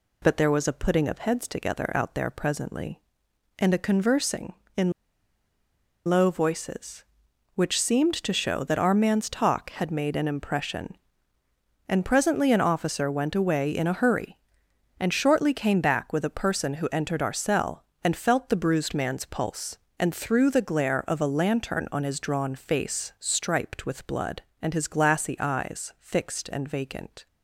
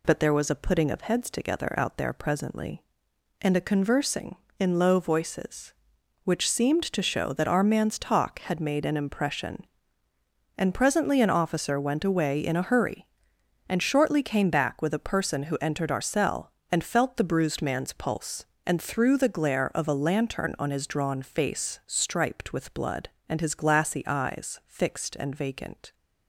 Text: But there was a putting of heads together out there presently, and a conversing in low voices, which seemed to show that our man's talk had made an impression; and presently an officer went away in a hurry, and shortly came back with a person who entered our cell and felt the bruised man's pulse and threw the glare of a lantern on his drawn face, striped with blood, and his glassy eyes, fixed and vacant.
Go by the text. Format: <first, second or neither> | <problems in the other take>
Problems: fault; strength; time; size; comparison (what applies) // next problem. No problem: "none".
second | pauses between "in" and "low"; at 4.9 s; 1.1 s long